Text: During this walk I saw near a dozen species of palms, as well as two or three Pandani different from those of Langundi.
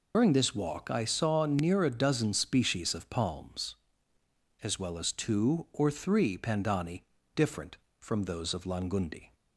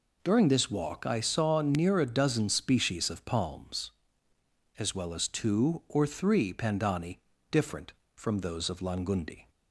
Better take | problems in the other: second | loses the start of "During"; at 0.1 s; 85 ms // pauses between "Pandani" and "different"; slight; at 7.0 s; 0.32 s long; slight in the second

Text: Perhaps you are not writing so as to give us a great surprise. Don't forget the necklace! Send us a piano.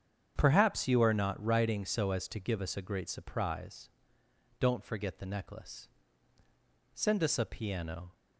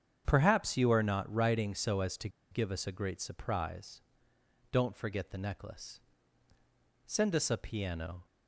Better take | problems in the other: first | starts louder than the rest; strong; until 1.2 s; 8 dB; strong in the first // pauses between "to" and "give"; slight; at 2.2 s; 0.23 s long

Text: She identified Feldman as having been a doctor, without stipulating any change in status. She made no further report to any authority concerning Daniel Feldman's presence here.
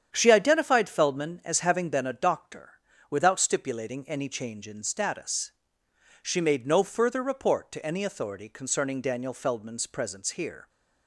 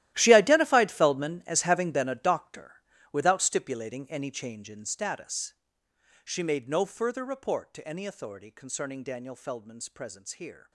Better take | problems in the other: first | gets quieter; strong; throughout; 17 dB // starts louder than the rest; strong; until 1.1 s; 14.5 dB; strong in the first

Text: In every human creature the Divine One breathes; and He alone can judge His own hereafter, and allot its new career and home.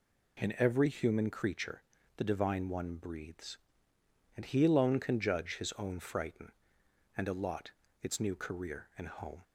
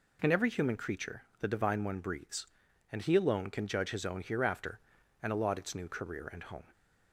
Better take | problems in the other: second | pauses between "creature" and "the"; slight; at 1.8 s; 0.34 s long; slight in the second // says "frighten" for "hereafter"; at 5.9 s // pauses between "allot" and "its"; slight; at 7.7 s; 0.30 s long

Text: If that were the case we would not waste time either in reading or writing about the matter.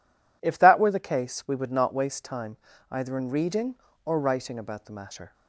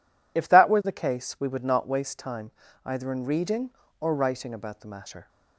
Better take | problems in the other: first | loses the start of "If"; at 0.3 s; 40 ms // pauses between "time" and "either"; slight; at 2.5 s; 0.34 s long; slight in the first

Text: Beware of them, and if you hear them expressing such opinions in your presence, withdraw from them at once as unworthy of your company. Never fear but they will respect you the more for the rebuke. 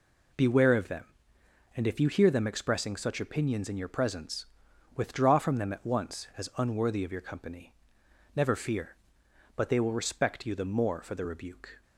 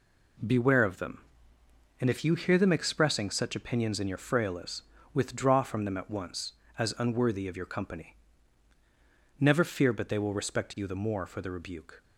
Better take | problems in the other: first | says "frailes" for "presence"; at 4.1 s

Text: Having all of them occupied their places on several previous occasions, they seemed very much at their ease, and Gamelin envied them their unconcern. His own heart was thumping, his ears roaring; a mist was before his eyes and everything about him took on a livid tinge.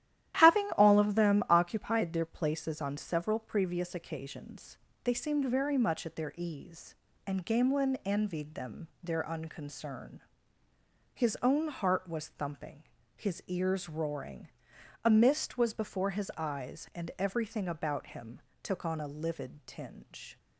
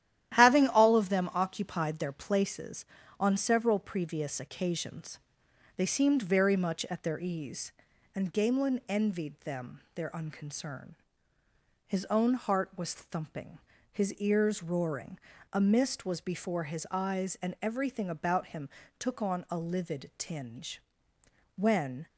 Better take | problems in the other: first | starts louder than the rest; strong; until 1.3 s; 12 dB; strong in the first // pauses between "him" and "took"; slight; at 18.7 s; 0.28 s long; slight in the first // goes on to say "When"; from 21.5 s on; 0.50 s long

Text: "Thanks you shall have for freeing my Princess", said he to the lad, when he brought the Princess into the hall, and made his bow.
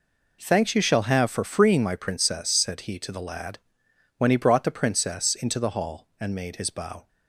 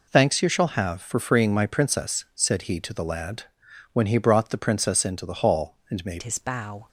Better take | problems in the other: first | changes voice at "his"; from 6.2 s on; 0.6 s long

